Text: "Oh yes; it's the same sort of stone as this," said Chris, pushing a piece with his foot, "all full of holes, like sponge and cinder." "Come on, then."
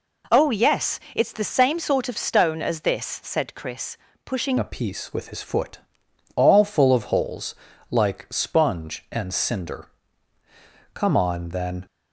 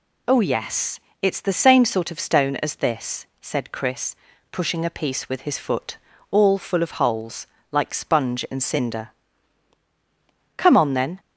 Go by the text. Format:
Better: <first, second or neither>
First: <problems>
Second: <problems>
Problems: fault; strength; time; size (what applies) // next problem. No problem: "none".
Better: second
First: changes voice at "a"; from 4.5 s on; 7.3 s long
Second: none